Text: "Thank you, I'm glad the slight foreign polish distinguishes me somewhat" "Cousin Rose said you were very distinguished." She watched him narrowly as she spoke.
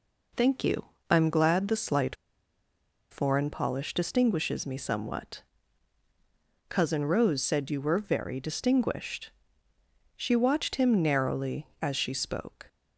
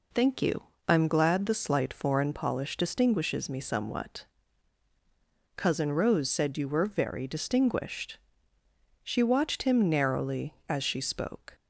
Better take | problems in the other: second | pauses between "slight" and "foreign"; noticeable; at 2.1 s; 0.95 s long // pauses between "somewhat" and "Cousin"; strong; at 5.4 s; 1.2 s long; strong in the second

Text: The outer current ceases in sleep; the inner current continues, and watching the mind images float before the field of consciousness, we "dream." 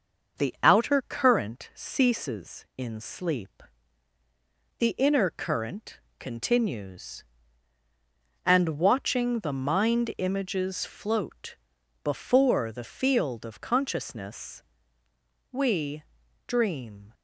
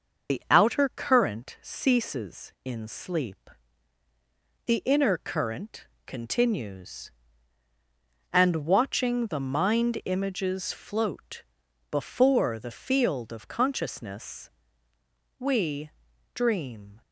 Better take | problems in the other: first | loses the start of "The"; at 0.2 s; 55 ms // starts louder than the rest; noticeable; until 1.3 s; 6 dB; noticeable in the first // pauses between "current" and "continues"; slight; at 5.8 s; 0.20 s long; slight in the first // pauses between "float" and "before"; noticeable; at 11.4 s; 0.48 s long; noticeable in the first // pauses between "we" and "dream"; at 15.9 s; 0.44 s long; also in the first

